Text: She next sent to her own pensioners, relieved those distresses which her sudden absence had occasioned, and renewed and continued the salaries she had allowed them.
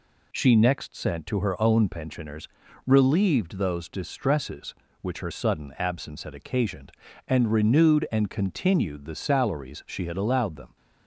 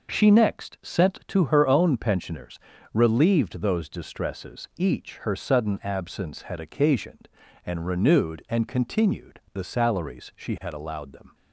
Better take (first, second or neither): first